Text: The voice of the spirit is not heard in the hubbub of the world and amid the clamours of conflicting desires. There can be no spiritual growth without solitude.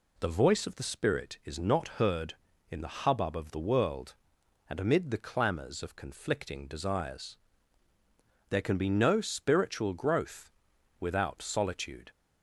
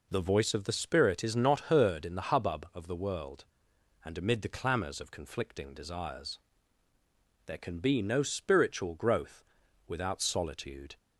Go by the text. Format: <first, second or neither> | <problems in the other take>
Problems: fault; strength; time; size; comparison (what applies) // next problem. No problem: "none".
neither | pauses between "growth" and "without"; the same in both